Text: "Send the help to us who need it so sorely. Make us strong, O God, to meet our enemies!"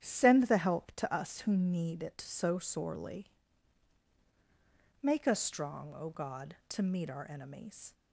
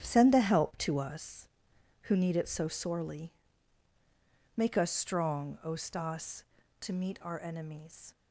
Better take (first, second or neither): first